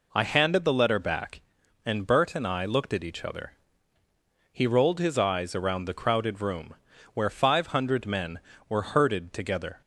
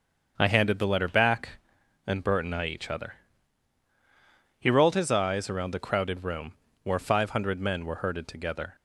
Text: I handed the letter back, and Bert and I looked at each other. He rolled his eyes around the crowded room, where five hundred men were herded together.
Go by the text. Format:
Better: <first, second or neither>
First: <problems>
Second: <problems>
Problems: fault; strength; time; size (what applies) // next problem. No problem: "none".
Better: first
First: none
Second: starts louder than the rest; until 1.3 s; 7 dB // skips "looked at"; at 2.6 s